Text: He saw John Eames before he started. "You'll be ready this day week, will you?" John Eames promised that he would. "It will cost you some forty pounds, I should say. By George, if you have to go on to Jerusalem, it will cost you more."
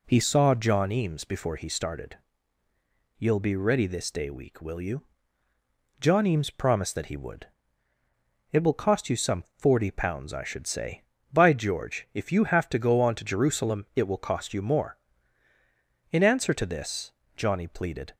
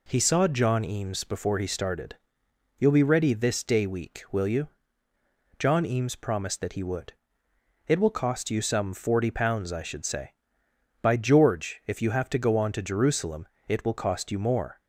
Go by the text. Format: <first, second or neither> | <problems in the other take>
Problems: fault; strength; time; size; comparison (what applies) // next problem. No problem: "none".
second | goes on to say "In answer to this Johnny pleaded"; strong; from 16.1 s on; 2.0 s long